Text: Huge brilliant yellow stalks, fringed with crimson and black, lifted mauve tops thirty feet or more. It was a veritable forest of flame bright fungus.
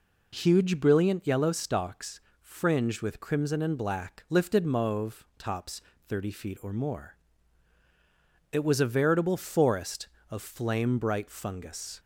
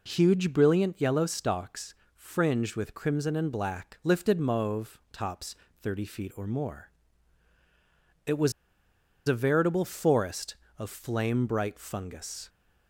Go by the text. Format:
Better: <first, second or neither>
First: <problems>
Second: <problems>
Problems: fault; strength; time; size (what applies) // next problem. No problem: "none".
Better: first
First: pauses between "tops" and "thirty"; slight; at 5.8 s; 0.26 s long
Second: pauses between "tops" and "thirty"; slight; at 5.5 s; 0.26 s long // pauses between "was" and "a"; noticeable; at 8.5 s; 0.76 s long